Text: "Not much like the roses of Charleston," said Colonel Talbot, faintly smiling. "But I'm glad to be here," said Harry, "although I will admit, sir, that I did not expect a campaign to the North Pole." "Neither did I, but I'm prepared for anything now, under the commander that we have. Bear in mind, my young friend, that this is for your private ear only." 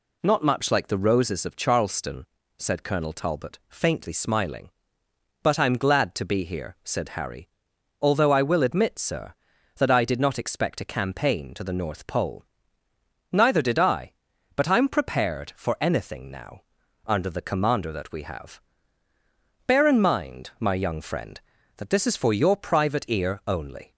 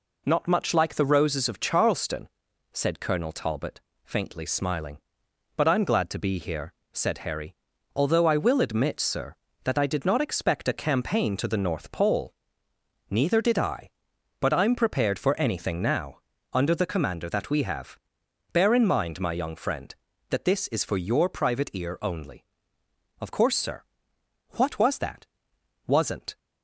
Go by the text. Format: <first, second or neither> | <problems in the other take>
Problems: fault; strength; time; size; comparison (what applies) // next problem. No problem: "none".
first | goes on to say "Of course sir What was that Wasn't"; strong; from 23.1 s on; 3.1 s long